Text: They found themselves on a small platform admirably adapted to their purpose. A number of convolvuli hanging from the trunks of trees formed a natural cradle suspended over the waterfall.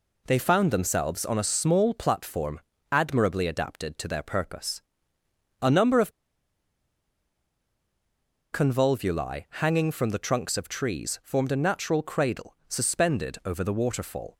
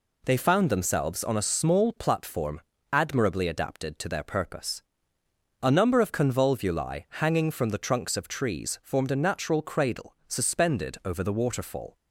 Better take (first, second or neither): second